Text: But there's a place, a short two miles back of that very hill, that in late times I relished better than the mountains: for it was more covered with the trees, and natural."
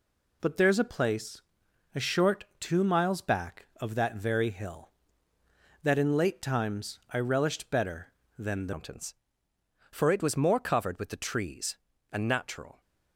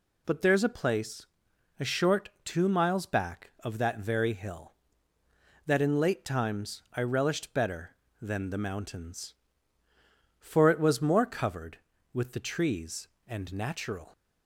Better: second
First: changes voice at "mountains"; from 8.7 s on; 4.1 s long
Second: none

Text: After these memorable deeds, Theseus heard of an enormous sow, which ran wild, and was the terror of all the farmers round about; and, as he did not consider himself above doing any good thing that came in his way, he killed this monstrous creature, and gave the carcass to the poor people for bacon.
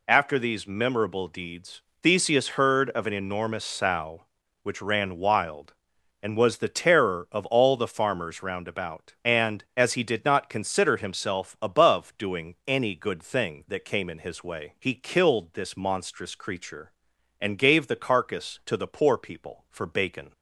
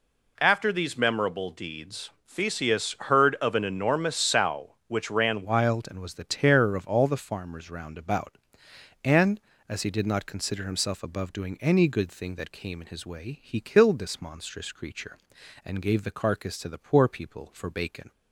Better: first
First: none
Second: changes voice at "wild"; from 5.4 s on; 12.7 s long

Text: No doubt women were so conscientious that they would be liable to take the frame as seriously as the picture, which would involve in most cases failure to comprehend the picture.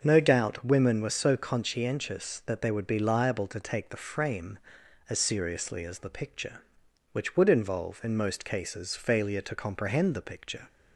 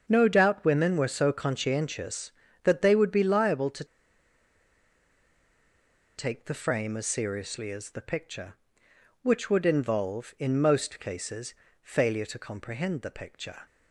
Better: first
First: starts louder than the rest; noticeable; until 1.0 s; 6 dB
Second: starts louder than the rest; until 1.0 s; 7 dB // pauses between "to" and "take"; strong; at 3.8 s; 2.3 s long // pauses between "cases" and "failure"; slight; at 11.5 s; 0.28 s long

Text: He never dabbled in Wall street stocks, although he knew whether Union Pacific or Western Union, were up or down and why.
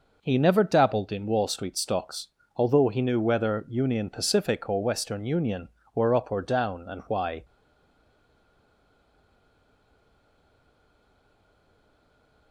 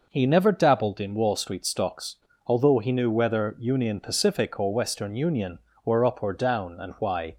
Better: second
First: stays silent after the last word; strong; from 7.4 s on; 5.1 s long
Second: none

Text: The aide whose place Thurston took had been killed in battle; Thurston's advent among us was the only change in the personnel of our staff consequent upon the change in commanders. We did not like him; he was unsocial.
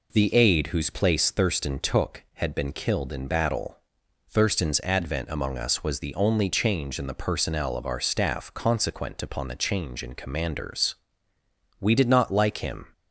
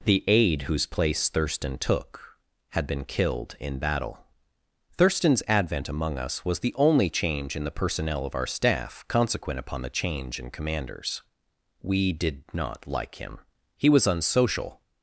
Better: second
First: stops before "he was unsocial"; at 12.9 s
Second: none

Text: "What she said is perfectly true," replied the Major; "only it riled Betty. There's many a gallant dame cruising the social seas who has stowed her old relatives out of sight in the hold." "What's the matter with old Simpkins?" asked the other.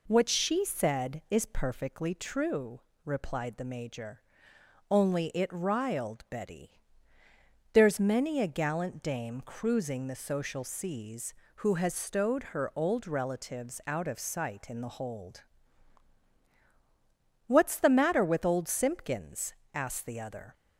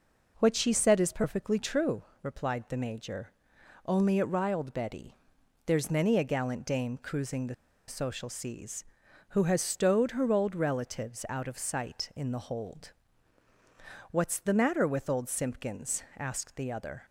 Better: first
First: none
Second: pauses between "the" and "social"; slight; at 7.5 s; 0.33 s long

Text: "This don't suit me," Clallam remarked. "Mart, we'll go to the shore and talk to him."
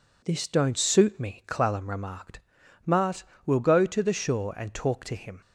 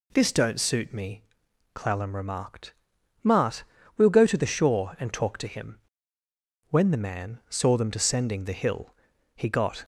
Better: first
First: none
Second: goes on to say "When the man saw them descending the hill he got"; strong; from 6.6 s on; 3.1 s long

